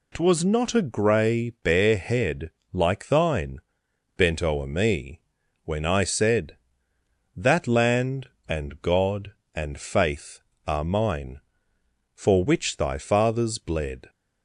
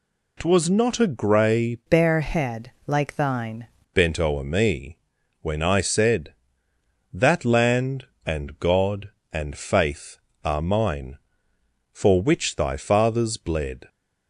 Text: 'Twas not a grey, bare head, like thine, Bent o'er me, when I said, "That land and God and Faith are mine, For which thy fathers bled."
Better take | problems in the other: first | changes voice from "bare" to "thine"; from 1.8 to 3.6 s; 1.8 s long

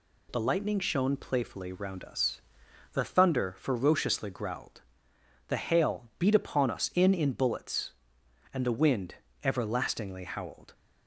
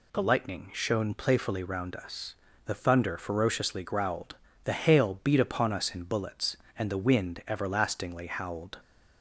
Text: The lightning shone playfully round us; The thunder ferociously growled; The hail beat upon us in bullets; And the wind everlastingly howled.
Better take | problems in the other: second | says "in" twice; at 7.1 s // pauses between "wind" and "everlastingly"; slight; at 9.1 s; 0.26 s long

